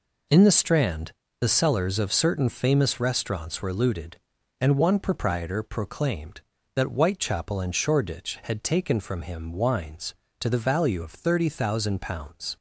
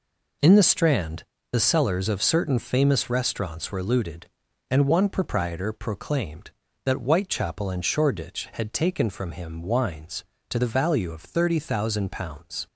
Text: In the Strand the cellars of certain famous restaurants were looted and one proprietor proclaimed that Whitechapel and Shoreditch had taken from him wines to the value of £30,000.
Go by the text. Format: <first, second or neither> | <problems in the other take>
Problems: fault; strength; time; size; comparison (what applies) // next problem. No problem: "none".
neither | pauses between "Strand" and "the"; slight; the same in both